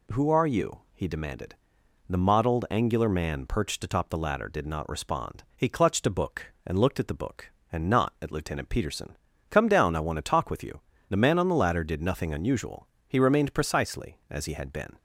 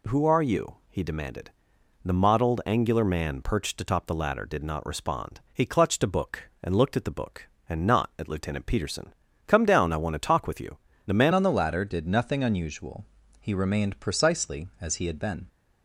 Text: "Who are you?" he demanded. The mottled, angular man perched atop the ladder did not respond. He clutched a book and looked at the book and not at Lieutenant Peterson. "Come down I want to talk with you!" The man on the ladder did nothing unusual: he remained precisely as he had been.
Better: first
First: none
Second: changes voice at "on"; from 11.3 s on; 4.1 s long

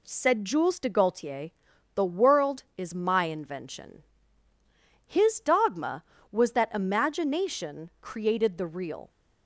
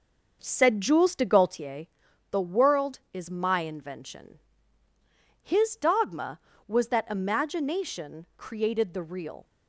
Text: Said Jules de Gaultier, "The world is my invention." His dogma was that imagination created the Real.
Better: first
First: none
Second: starts louder than the rest; noticeable; until 1.7 s; 6 dB

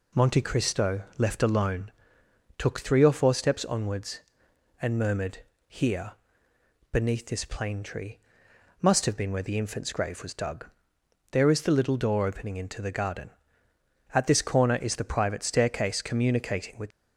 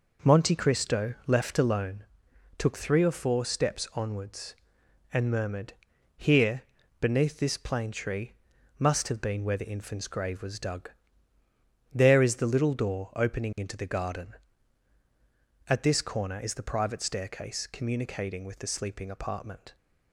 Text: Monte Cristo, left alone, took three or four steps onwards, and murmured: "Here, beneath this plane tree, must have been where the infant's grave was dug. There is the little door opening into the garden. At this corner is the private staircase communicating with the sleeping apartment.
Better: second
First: stops before "the sleeping apartment"; at 16.9 s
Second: none

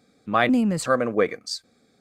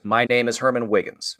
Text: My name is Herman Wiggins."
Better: second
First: changes voice from "name" to "is"; from 0.4 to 0.8 s; 0.4 s long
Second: none

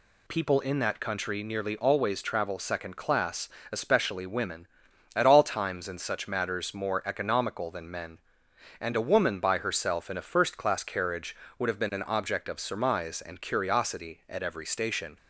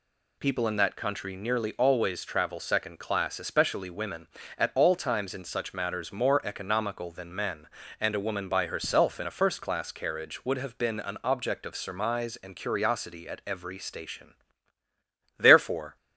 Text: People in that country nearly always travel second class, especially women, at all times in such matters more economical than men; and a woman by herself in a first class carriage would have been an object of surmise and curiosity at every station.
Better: first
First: none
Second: goes on to say "Therefore"; from 15.3 s on; 0.58 s long

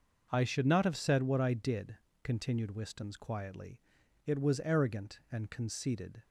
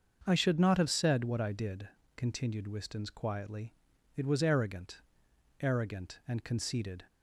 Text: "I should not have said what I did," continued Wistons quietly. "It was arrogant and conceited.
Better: first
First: starts louder than the rest; noticeable; until 1.3 s; 6 dB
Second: starts louder than the rest; until 1.2 s; 6.5 dB // says "arrogant" twice; at 5.5 s

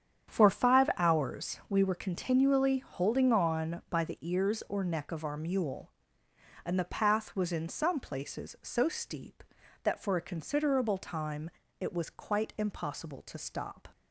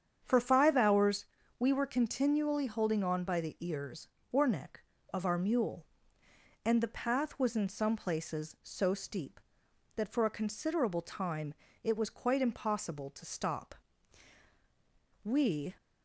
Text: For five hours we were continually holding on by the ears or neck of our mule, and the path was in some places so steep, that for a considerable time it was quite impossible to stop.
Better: first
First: starts louder than the rest; strong; until 1.3 s; 8.5 dB // pauses between "time" and "it"; slight; at 11.4 s; 0.32 s long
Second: starts louder than the rest; strong; until 1.2 s; 8 dB // pauses between "hours" and "we"; slight; at 1.2 s; 0.34 s long // pauses between "time" and "it"; slight; at 11.5 s; 0.30 s long // goes on to say "We"; from 15.2 s on; 0.52 s long

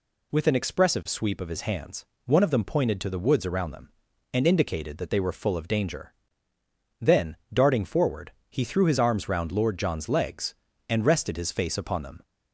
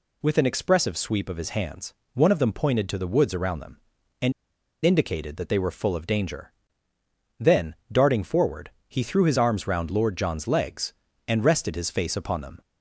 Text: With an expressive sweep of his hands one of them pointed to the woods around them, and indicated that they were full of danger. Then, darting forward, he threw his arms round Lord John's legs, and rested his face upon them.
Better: first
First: pauses between "hands" and "one"; slight; at 2.0 s; 0.22 s long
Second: pauses between "hands" and "one"; slight; at 1.9 s; 0.22 s long // pauses between "and" and "indicated"; noticeable; at 4.3 s; 0.52 s long

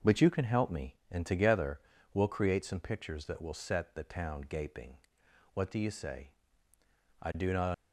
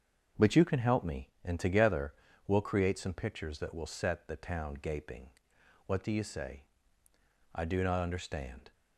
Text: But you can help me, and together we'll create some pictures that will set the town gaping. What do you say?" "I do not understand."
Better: second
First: starts louder than the rest; noticeable; until 1.2 s; 6 dB // pauses between "together" and "we'll"; slight; at 1.7 s; 0.34 s long // stops before "understand"; at 7.7 s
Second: starts louder than the rest; until 1.5 s; 6.5 dB // pauses between "together" and "we'll"; slight; at 2.1 s; 0.34 s long

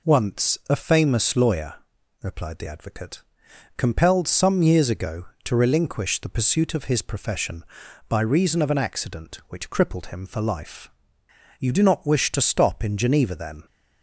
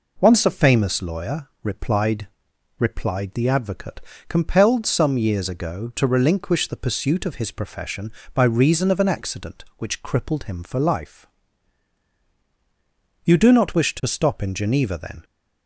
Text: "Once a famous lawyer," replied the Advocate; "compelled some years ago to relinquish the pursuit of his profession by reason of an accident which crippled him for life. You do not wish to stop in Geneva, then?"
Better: first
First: none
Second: says "replied" twice; at 2.7 s

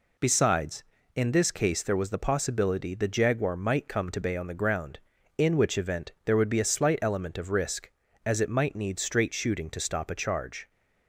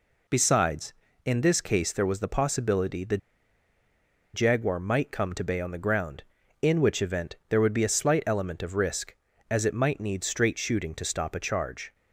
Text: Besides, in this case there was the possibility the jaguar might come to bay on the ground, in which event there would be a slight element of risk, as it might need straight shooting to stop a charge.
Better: first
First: none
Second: pauses between "the" and "jaguar"; at 3.1 s; 1.1 s long

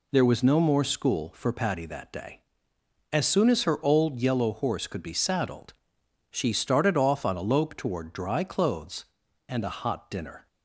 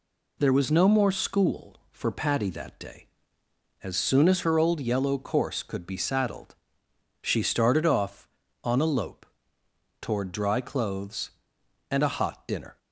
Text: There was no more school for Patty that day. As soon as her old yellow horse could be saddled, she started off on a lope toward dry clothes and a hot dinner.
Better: first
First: none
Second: says "course" for "horse"; at 5.1 s // pauses between "lope" and "toward"; noticeable; at 9.2 s; 0.74 s long

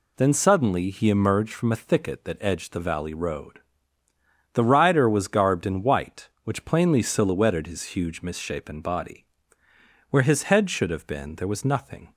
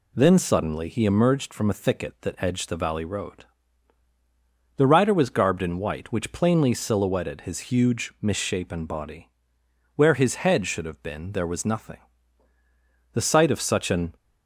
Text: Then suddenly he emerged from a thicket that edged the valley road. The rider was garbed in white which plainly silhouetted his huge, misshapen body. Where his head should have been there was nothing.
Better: first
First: none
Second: goes on to say "The sight of such an"; noticeable; from 13.1 s on; 1.0 s long

